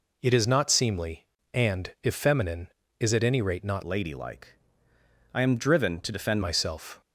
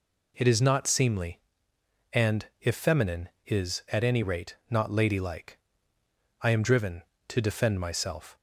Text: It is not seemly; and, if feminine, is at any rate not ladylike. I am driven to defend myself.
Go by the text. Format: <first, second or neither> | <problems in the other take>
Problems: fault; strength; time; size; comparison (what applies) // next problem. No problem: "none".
second | changes voice from "ladylike" to "defend"; from 3.8 to 6.4 s; 2.6 s long